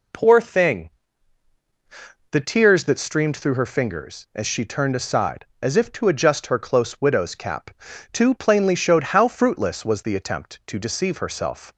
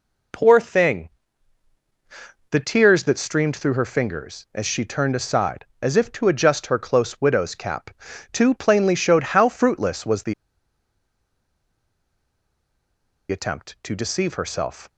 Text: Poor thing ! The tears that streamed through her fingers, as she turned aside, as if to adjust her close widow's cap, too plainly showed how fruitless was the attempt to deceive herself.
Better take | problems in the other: first | pauses between "the" and "attempt"; strong; at 10.3 s; 2.9 s long

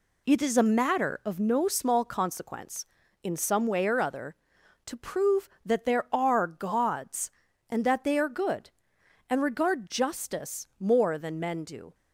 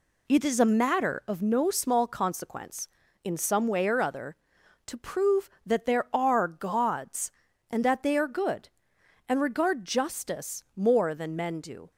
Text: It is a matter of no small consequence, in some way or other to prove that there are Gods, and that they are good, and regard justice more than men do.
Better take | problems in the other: neither | none

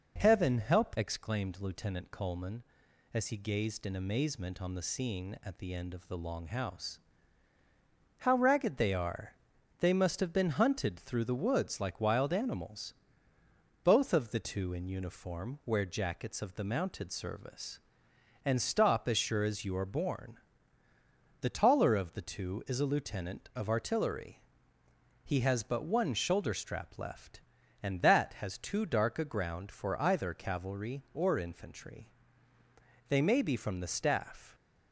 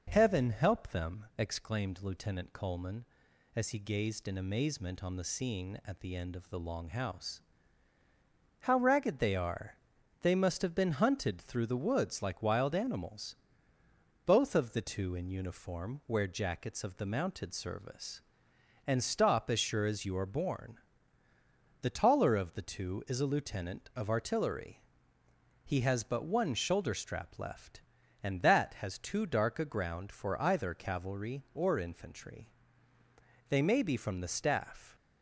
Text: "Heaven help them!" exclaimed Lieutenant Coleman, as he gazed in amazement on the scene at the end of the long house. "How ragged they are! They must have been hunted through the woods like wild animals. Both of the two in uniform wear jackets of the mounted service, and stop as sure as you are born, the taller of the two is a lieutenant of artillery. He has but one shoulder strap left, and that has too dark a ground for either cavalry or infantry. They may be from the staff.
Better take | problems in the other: second | skips "them"; at 0.9 s

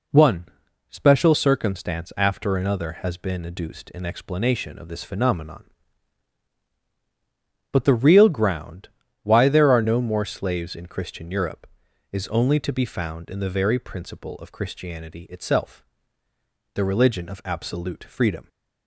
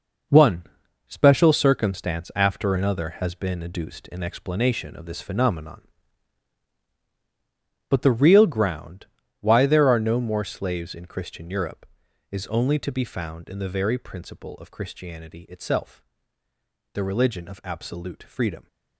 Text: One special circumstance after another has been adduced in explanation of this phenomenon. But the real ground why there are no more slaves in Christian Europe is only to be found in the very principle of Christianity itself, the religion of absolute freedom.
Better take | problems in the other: first | gets quieter; strong; throughout; 9 dB // pauses between "One" and "special"; at 0.6 s; 0.42 s long; also in the first // pauses between "ground" and "why"; slight; at 9.0 s; 0.34 s long; slight in the first

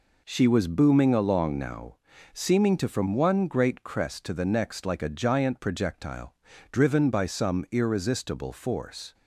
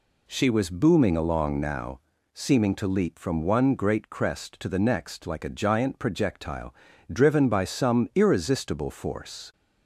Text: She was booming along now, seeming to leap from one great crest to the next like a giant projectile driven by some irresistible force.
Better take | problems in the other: second | skips "leap"; at 2.8 s // pauses between "projectile" and "driven"; at 6.3 s; 0.38 s long; also in the second

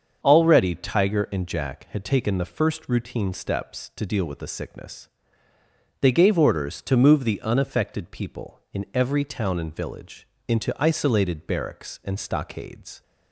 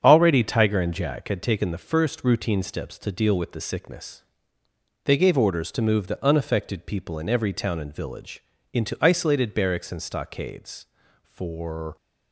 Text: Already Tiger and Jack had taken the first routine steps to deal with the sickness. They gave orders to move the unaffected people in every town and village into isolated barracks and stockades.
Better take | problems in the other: first | starts louder than the rest; strong; until 1.0 s; 8 dB; also in the first // pauses between "village" and "into"; slight; at 8.4 s; 0.30 s long; slight in the first // goes on to say "For"; noticeable; from 11.2 s on; 0.72 s long

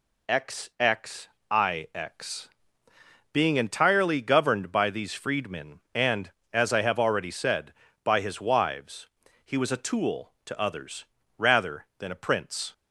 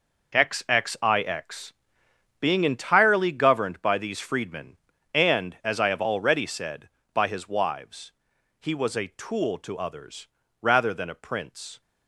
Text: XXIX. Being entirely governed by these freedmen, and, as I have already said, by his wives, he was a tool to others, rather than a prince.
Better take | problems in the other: first | gets quieter; strong; throughout; 10 dB

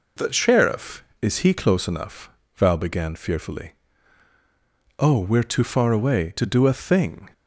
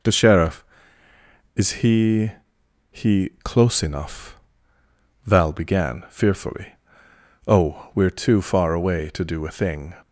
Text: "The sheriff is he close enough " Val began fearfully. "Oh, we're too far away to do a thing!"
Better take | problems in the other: first | says "he" twice; at 2.9 s

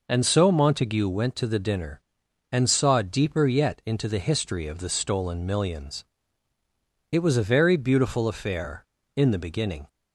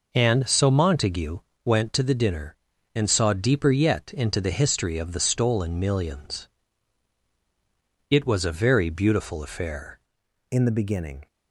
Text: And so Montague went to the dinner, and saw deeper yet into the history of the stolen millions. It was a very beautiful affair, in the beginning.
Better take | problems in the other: first | pauses between "Montague" and "went"; slight; at 1.3 s; 0.26 s long // changes voice at "in"; from 10.5 s on; 0.7 s long

